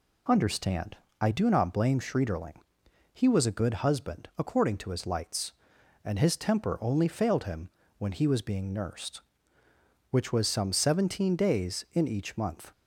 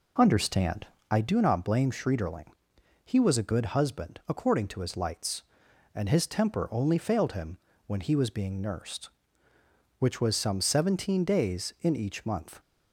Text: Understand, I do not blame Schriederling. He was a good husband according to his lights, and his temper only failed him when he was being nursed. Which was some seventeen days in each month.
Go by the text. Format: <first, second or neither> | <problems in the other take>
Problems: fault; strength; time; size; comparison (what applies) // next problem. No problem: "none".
first | starts louder than the rest; until 1.2 s; 3.5 dB // pauses between "him" and "when"; slight; at 7.5 s; 0.30 s long; slight in the first